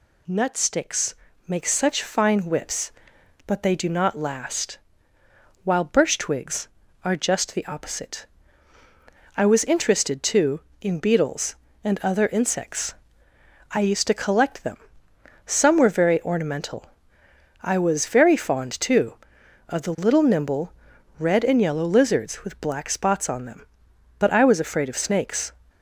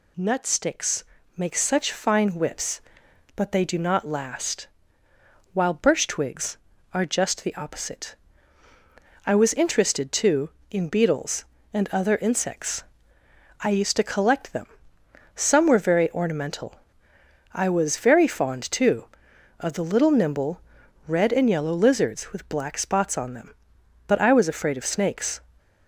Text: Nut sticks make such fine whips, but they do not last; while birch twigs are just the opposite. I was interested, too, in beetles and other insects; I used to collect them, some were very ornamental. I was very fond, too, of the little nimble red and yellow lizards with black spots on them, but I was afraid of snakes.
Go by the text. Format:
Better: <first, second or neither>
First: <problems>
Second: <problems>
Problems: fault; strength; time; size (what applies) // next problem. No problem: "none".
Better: neither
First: pauses between "sticks" and "make"; slight; at 1.1 s; 0.34 s long // pauses between "nimble" and "red"; noticeable; at 20.7 s; 0.46 s long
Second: pauses between "sticks" and "make"; slight; at 1.0 s; 0.34 s long // pauses between "nimble" and "red"; noticeable; at 20.6 s; 0.46 s long